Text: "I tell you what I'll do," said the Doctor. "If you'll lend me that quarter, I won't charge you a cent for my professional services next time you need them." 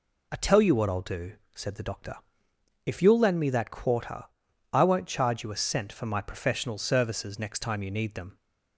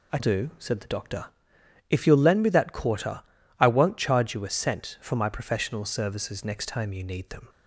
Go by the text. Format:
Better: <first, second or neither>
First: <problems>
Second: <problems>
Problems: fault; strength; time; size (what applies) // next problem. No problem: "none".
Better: first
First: none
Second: skips "tell you what I'll"; at 0.1 s